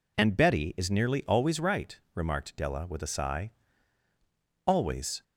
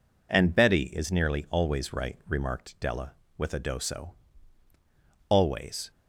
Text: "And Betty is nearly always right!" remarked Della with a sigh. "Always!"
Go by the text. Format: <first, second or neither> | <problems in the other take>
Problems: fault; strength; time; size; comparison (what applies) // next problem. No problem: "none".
first | says "doso" for "sigh"; at 3.5 s